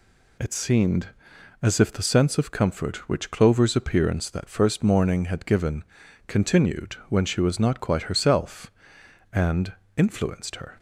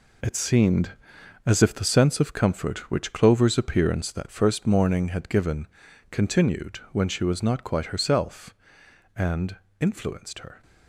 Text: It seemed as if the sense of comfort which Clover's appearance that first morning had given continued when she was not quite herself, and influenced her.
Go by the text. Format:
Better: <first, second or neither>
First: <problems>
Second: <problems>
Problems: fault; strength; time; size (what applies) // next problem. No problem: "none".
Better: first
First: pauses between "given" and "continued"; at 5.8 s; 0.44 s long // pauses between "and" and "influenced"; slight; at 9.7 s; 0.24 s long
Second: gets quieter; strong; throughout; 9 dB // pauses between "given" and "continued"; at 5.6 s; 0.44 s long // pauses between "and" and "influenced"; slight; at 9.5 s; 0.24 s long